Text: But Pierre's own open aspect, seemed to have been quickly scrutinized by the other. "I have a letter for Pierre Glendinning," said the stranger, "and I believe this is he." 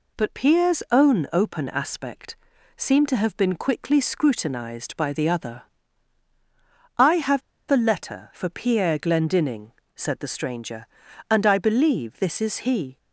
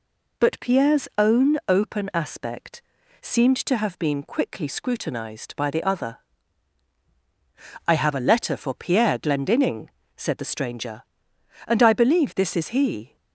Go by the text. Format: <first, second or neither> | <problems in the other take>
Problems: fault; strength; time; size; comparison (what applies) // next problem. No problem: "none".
second | pauses between "have" and "a"; slight; at 7.4 s; 0.29 s long